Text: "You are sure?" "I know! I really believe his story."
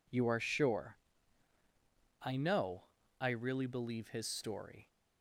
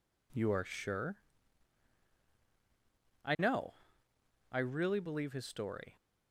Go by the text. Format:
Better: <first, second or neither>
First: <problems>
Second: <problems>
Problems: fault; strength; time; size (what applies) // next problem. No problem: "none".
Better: neither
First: none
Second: none